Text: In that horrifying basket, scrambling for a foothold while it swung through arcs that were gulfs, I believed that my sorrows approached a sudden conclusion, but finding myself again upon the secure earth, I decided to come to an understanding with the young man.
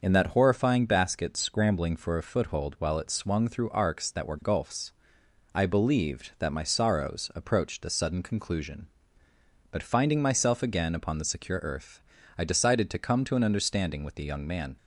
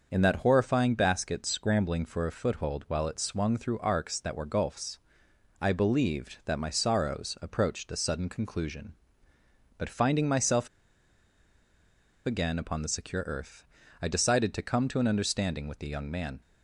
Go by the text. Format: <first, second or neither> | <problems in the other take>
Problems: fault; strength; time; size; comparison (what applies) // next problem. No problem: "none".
first | starts louder than the rest; until 1.1 s; 6.5 dB; also in the first // pauses between "myself" and "again"; strong; at 10.6 s; 1.5 s long